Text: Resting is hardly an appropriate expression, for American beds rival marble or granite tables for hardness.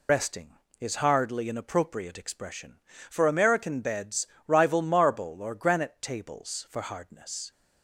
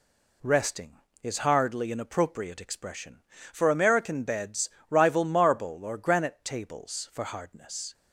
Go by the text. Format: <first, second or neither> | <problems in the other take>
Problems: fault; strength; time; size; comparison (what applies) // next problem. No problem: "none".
second | loses the start of "Resting"; at 0.0 s; 110 ms // pauses between "beds" and "rival"; slight; at 4.2 s; 0.18 s long; slight in the second